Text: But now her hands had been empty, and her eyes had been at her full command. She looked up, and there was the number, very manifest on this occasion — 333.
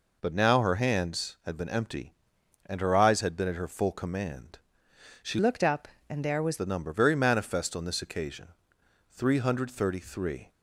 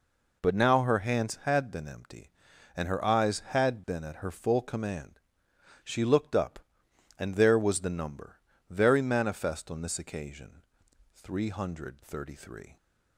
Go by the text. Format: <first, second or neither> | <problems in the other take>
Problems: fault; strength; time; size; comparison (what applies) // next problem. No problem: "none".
second | changes voice from "looked" to "was"; from 5.3 to 6.5 s; 1.2 s long